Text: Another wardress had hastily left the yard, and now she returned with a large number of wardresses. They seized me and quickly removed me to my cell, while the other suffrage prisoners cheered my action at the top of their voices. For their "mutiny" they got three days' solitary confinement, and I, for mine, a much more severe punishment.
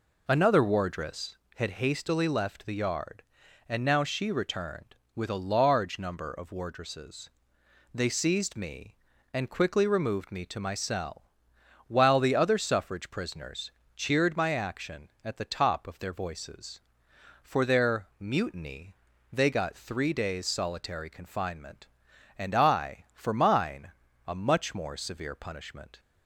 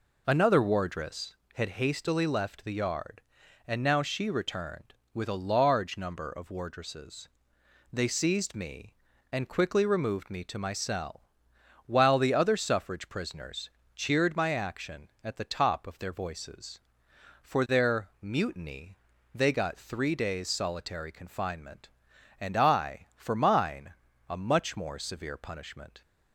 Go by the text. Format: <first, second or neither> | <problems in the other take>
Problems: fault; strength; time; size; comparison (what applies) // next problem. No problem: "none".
neither | pauses between "prisoners" and "cheered"; slight; the same in both // pauses between "mutiny" and "they"; slight; the same in both